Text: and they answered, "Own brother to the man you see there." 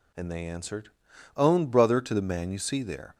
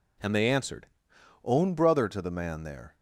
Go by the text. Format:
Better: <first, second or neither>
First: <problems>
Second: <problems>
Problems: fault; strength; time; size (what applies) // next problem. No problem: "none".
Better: first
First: none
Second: skips "you see"; at 2.6 s